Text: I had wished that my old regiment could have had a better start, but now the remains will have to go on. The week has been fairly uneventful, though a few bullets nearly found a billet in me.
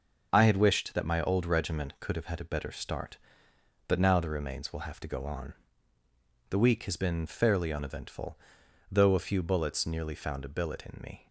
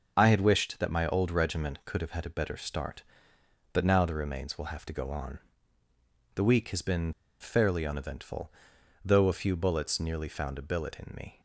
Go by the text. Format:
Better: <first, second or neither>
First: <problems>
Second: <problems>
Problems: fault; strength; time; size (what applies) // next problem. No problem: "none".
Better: first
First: none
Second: pauses between "been" and "fairly"; slight; at 7.1 s; 0.27 s long